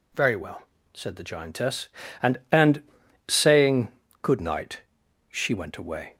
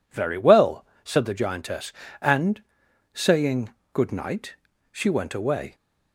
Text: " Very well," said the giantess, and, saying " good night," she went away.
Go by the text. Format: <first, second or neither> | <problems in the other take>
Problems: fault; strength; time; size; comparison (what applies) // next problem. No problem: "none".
second | says "and" twice; at 2.5 s